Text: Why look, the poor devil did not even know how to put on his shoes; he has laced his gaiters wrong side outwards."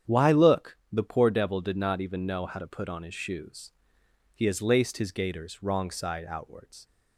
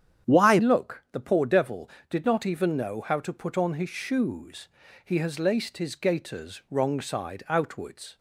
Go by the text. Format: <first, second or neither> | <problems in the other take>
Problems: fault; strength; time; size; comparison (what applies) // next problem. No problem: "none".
first | starts louder than the rest; strong; until 1.3 s; 9 dB; strong in the first // changes voice at "look"; from 0.5 s on; 7.6 s long